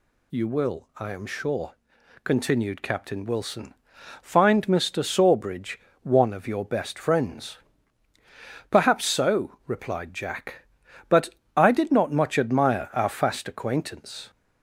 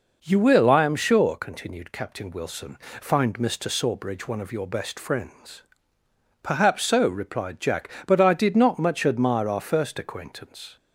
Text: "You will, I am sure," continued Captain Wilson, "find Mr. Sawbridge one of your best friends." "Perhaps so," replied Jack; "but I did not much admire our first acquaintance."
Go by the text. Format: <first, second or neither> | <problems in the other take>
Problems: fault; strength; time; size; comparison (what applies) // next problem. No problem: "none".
second | pauses between "Sawbridge" and "one"; slight; at 5.8 s; 0.24 s long // pauses between "but" and "I"; slight; at 11.3 s; 0.26 s long // says "fast" for "first"; at 13.0 s